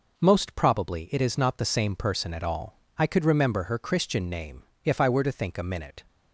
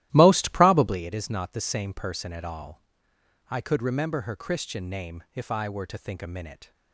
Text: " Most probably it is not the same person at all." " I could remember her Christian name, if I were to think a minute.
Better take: first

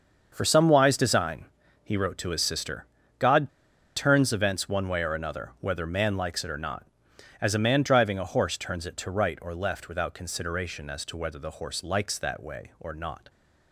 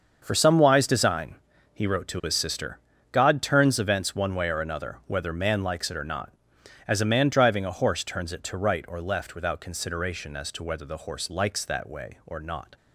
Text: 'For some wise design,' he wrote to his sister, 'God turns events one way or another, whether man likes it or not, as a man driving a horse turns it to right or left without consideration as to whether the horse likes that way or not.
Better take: second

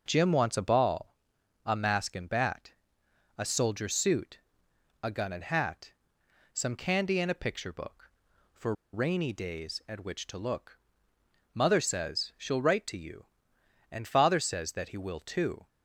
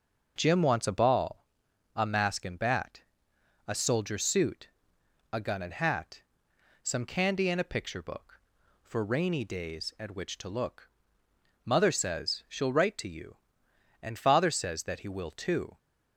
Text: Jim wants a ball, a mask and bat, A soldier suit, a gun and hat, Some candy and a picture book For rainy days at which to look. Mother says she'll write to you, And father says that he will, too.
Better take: second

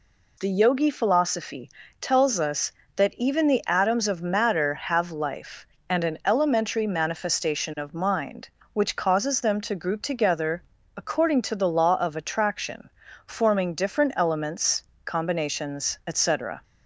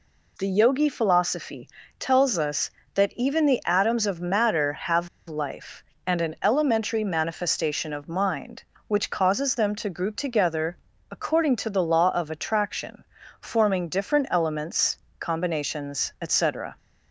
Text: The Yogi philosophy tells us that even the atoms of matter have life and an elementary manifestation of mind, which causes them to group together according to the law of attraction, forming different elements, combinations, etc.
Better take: first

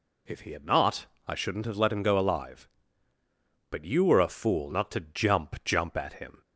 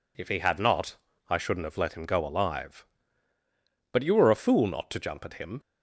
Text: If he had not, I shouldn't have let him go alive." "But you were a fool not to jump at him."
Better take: second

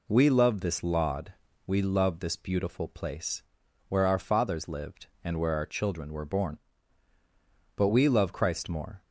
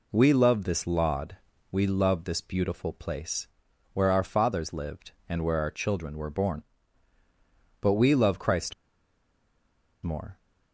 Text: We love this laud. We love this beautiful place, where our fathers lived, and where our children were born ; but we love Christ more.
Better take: first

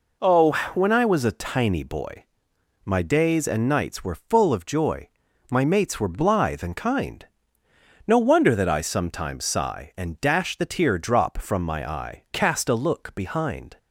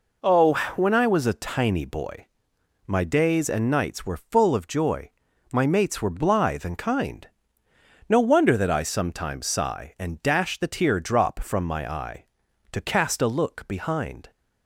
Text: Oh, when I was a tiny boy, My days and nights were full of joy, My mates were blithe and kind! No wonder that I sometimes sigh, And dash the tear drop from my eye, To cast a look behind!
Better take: second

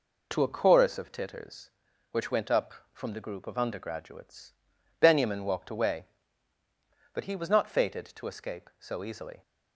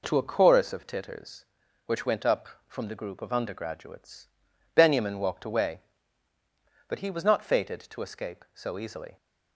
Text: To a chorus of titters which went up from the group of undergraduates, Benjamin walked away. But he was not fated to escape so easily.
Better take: second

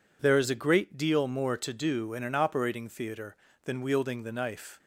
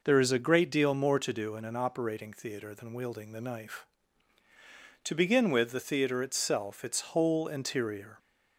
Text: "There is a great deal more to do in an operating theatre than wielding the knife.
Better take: first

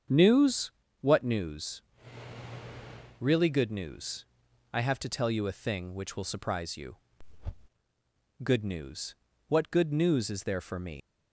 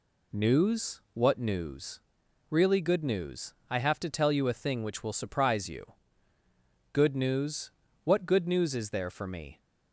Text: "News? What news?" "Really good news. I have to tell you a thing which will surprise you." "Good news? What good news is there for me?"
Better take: second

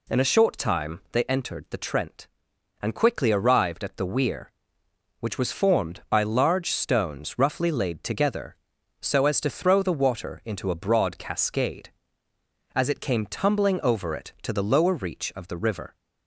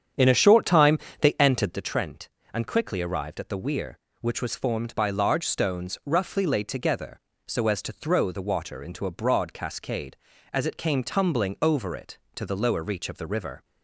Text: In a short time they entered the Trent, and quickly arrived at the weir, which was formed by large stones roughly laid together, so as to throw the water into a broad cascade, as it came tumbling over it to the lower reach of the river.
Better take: first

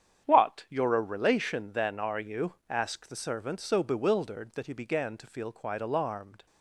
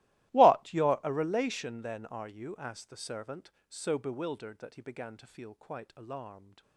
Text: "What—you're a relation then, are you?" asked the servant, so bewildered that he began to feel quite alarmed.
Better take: first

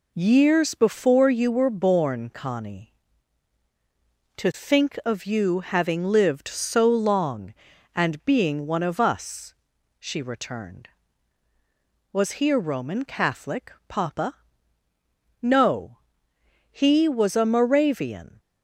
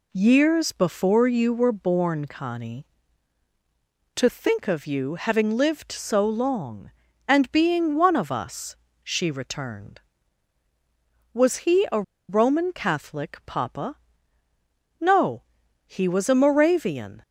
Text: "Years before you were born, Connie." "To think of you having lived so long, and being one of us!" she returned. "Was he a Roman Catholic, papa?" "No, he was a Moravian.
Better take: first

